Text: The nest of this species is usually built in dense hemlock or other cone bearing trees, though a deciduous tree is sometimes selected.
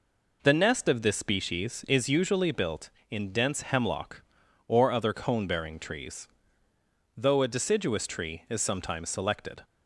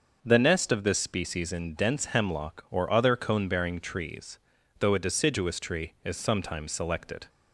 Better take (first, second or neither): first